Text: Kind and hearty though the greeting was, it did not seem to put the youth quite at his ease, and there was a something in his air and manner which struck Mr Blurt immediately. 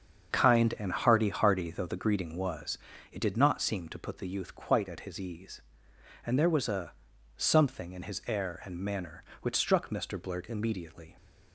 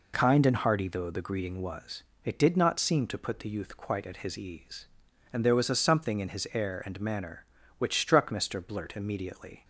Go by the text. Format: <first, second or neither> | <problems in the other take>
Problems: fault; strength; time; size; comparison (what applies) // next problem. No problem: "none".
second | starts louder than the rest; strong; until 1.3 s; 7 dB // says "hearty" twice; at 1.2 s // pauses between "a" and "something"; at 6.9 s; 0.44 s long